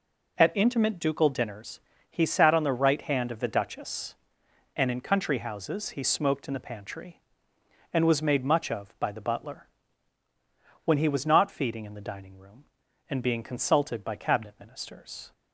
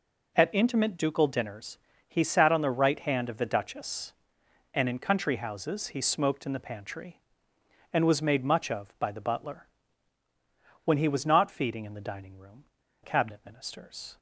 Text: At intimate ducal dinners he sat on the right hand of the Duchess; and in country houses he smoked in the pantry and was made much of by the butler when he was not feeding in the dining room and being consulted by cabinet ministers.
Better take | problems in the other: first | pauses between "dinners" and "he"; slight; at 1.7 s; 0.32 s long; slight in the first // pauses between "butler" and "when"; at 9.6 s; 1.1 s long; also in the first // skips "and being consulted by"; at 12.8 s

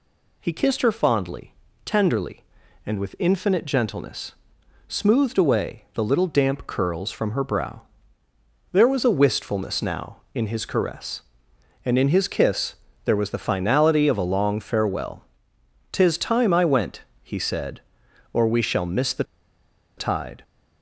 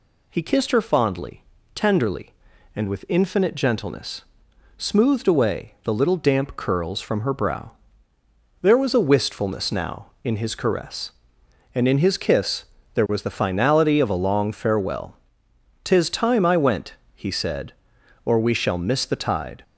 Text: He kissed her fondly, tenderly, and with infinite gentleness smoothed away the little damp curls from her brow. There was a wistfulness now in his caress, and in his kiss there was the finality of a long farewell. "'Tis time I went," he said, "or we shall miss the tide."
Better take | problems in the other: second | pauses between "gentleness" and "smoothed"; noticeable; at 4.3 s; 0.58 s long; noticeable in the second // pauses between "kiss" and "there"; slight; at 12.7 s; 0.30 s long; slight in the second // pauses between "the" and "tide"; noticeable; at 19.2 s; 0.74 s long

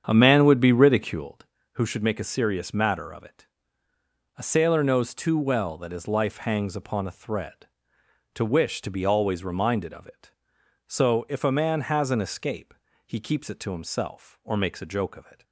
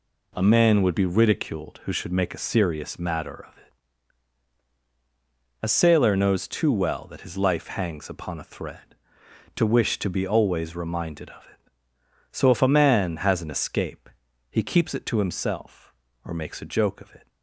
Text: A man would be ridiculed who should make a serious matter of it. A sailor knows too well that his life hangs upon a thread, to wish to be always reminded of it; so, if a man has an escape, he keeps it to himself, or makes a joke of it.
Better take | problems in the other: second | starts louder than the rest; strong; until 1.3 s; 8 dB

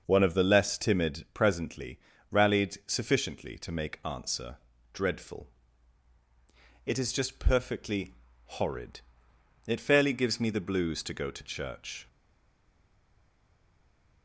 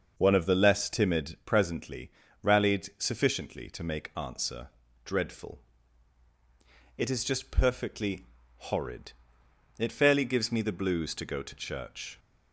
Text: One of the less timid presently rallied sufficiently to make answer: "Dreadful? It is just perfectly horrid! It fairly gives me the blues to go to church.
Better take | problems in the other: second | starts louder than the rest; until 1.0 s; 6 dB; also in the second // pauses between "presently" and "rallied"; slight; at 1.9 s; 0.32 s long; slight in the second // pauses between "perfectly" and "horrid"; noticeable; at 8.1 s; 0.46 s long; noticeable in the second // stays silent after the last word; from 12.0 s on; 2.2 s long

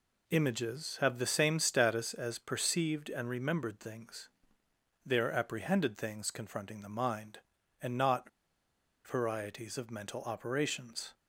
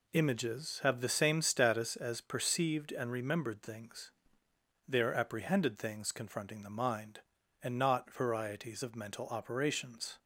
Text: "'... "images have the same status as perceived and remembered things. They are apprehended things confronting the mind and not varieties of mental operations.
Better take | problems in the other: second | pauses between "not" and "varieties"; noticeable; at 8.2 s; 0.77 s long

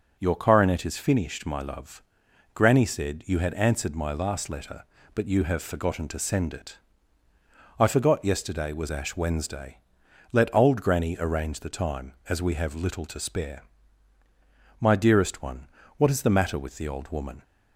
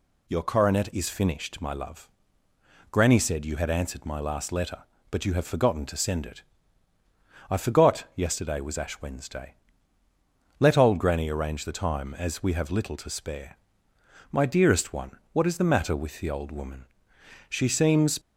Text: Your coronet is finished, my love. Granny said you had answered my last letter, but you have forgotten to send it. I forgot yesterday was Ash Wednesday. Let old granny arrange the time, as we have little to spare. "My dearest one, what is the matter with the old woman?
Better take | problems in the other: first | goes on to say "She seems"; noticeable; from 17.5 s on; 0.68 s long

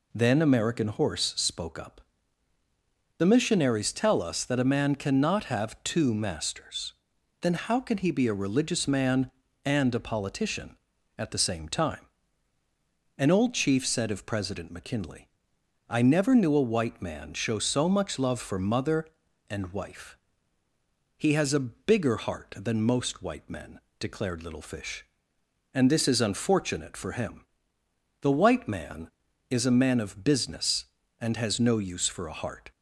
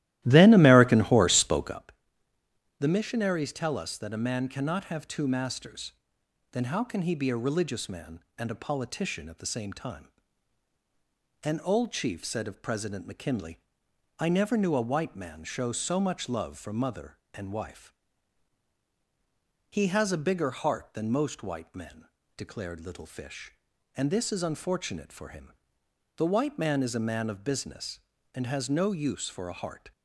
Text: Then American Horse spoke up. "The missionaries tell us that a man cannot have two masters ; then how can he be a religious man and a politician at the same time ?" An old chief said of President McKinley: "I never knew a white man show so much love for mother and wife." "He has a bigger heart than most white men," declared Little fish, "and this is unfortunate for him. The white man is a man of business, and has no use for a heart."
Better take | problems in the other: first | starts louder than the rest; strong; until 1.8 s; 15 dB

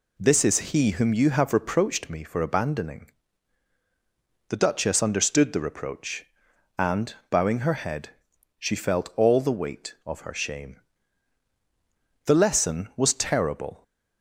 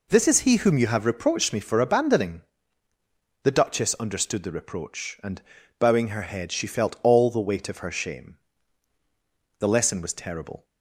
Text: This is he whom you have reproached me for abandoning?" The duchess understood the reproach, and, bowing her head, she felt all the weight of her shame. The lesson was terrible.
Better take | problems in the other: neither | none

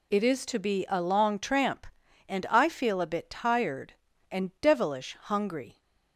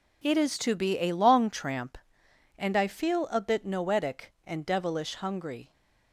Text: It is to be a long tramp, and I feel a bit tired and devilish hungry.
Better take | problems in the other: first | says "noetic" for "tired"; at 3.6 s

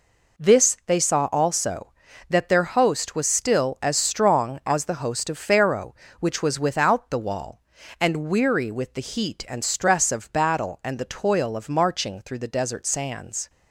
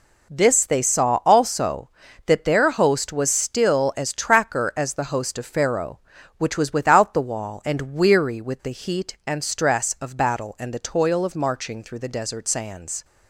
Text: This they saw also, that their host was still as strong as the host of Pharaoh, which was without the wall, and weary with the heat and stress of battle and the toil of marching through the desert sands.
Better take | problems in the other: first | says "tracker" for "strong"; at 4.1 s

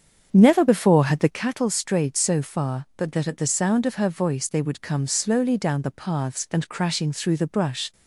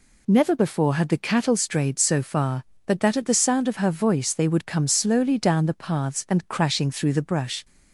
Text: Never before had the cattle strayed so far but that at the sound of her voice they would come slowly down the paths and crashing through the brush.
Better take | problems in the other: second | starts louder than the rest; strong; until 1.4 s; 7.5 dB

